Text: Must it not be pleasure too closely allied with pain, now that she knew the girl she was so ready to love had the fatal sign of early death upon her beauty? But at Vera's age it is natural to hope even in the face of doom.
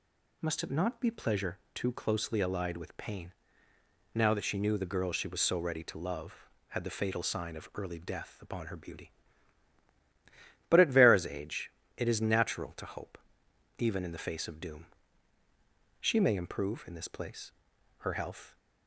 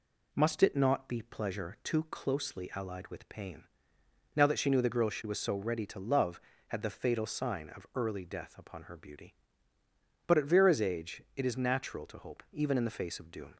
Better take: second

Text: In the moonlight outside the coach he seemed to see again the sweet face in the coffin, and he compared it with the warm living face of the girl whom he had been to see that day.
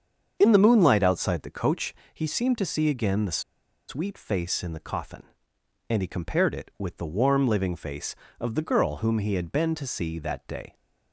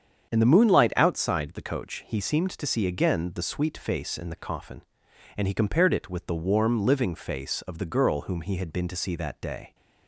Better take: second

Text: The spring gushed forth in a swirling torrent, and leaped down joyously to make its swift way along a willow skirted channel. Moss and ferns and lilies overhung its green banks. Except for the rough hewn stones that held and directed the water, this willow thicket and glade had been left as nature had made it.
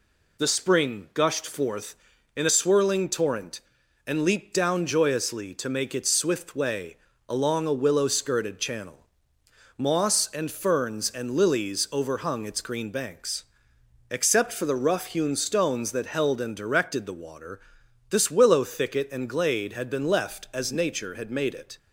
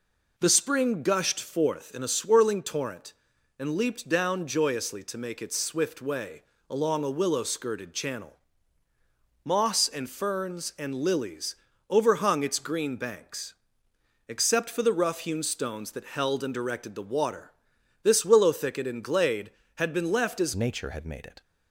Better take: first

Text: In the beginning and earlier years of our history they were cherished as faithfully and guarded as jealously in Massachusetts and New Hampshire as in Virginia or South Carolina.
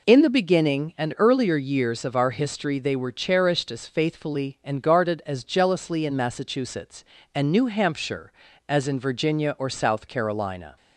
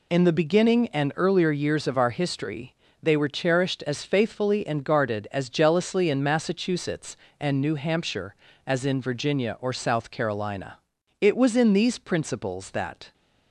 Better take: first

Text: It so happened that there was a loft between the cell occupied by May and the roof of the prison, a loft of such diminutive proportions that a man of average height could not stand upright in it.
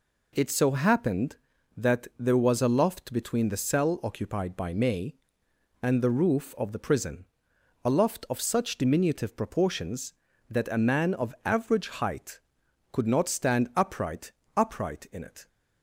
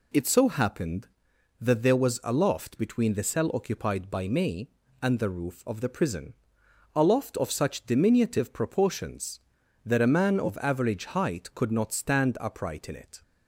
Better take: second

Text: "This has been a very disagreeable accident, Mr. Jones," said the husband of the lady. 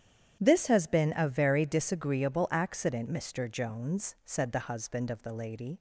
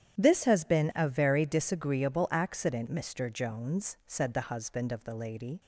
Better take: neither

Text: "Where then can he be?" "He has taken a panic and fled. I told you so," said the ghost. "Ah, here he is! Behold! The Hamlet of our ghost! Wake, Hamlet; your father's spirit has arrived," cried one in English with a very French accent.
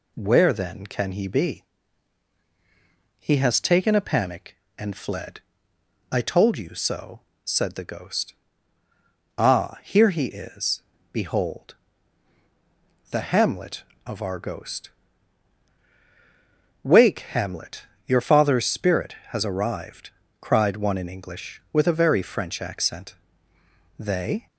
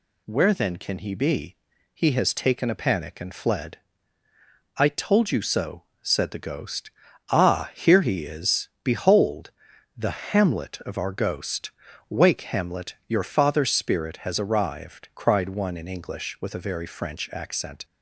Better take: second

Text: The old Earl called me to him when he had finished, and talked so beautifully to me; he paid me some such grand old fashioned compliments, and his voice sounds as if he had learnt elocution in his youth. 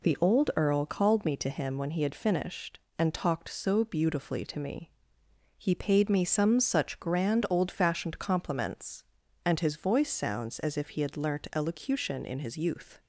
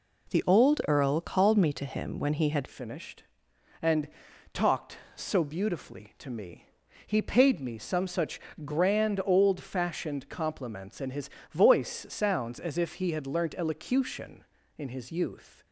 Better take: first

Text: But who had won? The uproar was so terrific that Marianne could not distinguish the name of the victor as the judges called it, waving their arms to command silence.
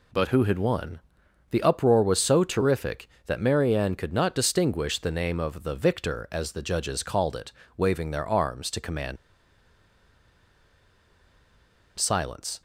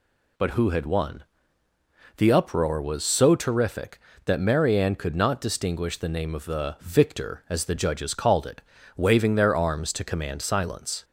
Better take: second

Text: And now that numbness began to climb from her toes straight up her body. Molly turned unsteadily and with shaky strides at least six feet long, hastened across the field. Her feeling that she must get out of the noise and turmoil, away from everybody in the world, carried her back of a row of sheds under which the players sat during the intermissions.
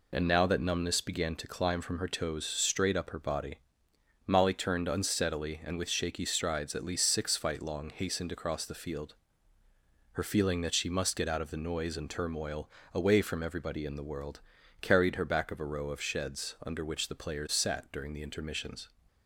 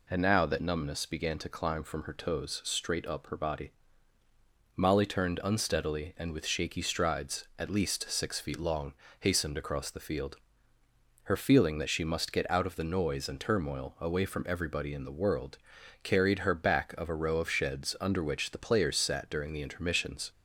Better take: second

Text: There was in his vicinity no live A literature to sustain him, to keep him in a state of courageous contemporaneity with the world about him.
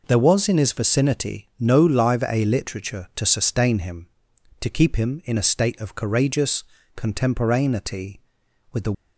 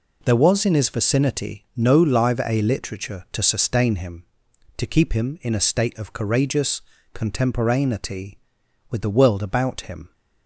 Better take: second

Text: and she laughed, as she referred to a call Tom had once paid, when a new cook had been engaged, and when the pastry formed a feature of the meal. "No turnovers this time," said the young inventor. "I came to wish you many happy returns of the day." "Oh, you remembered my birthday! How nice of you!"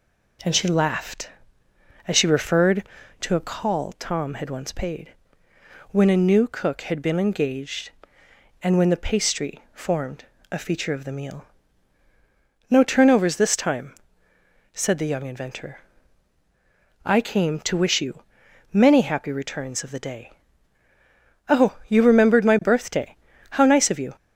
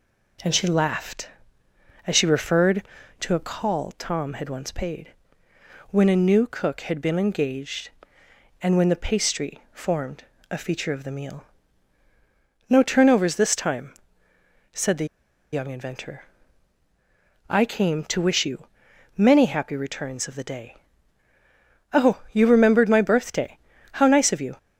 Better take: first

